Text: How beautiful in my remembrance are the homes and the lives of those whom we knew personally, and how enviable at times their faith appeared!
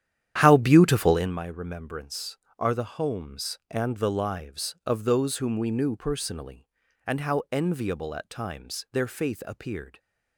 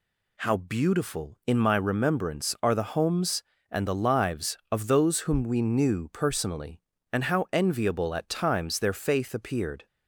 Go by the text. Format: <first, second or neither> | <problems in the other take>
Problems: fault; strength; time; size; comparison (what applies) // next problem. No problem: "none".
second | starts louder than the rest; strong; until 1.4 s; 10.5 dB